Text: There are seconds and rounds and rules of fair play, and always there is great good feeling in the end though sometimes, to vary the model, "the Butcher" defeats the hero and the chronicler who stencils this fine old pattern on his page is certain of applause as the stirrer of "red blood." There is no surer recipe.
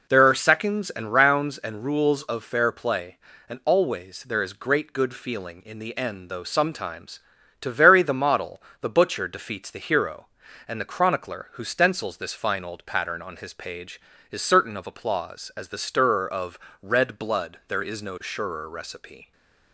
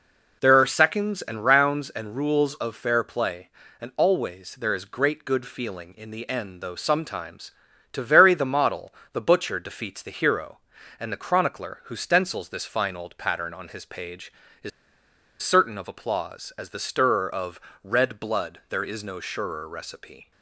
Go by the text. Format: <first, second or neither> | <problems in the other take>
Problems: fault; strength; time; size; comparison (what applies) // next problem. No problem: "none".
first | pauses between "is" and "certain"; noticeable; at 14.7 s; 0.72 s long // pauses between "of" and "red"; slight; at 17.6 s; 0.22 s long; slight in the first